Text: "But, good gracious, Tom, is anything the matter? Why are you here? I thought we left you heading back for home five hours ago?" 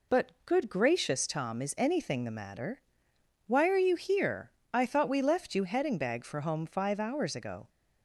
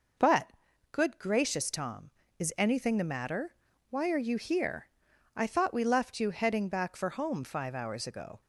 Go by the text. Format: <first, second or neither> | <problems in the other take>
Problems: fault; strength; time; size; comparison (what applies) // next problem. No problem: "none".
second | says "bag" for "back"; at 5.9 s